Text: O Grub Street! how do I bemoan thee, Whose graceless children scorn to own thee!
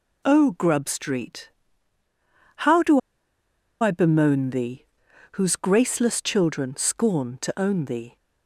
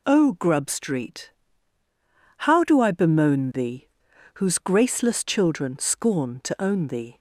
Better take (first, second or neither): second